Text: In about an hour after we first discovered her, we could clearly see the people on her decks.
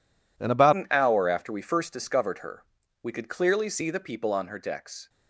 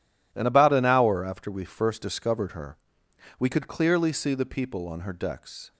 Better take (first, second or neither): second